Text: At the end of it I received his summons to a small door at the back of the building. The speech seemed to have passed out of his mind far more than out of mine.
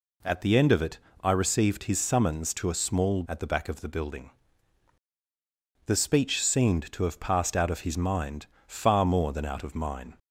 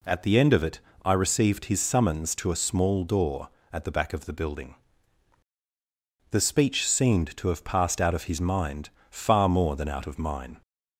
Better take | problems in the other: second | pauses between "it" and "I"; slight; at 0.9 s; 0.24 s long; slight in the second // skips "door"; at 3.2 s // pauses between "mind" and "far"; slight; at 8.4 s; 0.20 s long; slight in the second

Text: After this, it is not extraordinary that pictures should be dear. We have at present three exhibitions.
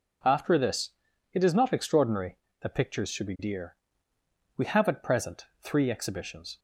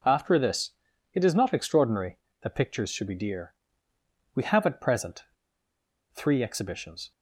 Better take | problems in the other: first | pauses between "present" and "three"; noticeable; at 5.2 s; 0.88 s long

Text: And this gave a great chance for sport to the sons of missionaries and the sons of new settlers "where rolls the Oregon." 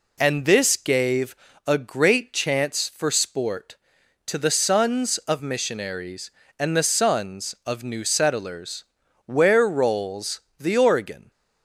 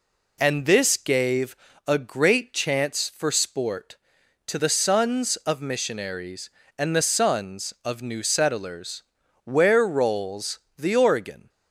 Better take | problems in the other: neither | pauses between "gave" and "a"; slight; the same in both // pauses between "settlers" and "where"; the same in both // pauses between "rolls" and "the"; slight; the same in both

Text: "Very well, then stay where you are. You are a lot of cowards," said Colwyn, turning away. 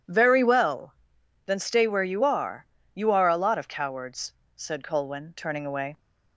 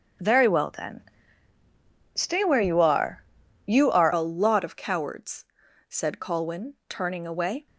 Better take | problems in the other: first | starts louder than the rest; until 2.3 s; 6.5 dB // pauses between "then" and "stay"; at 1.0 s; 1.1 s long // changes voice at "a"; from 4.1 s on; 3.5 s long

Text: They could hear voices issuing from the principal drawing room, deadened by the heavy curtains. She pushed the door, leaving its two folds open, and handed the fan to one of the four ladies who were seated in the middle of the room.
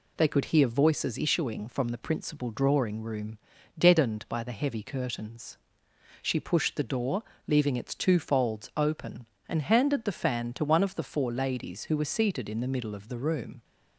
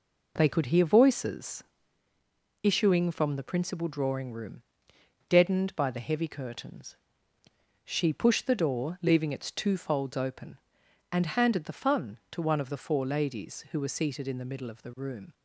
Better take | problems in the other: first | pauses between "voices" and "issuing"; at 1.6 s; 1.0 s long // says "fun" for "fan"; at 11.7 s

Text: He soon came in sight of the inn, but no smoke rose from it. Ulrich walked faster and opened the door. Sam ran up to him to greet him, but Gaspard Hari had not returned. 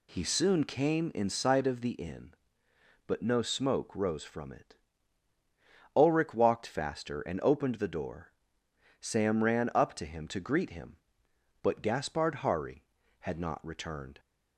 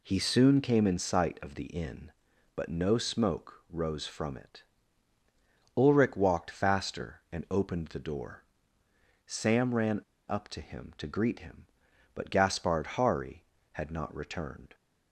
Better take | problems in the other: first | pauses between "ran" and "up"; slight; at 10.0 s; 0.28 s long

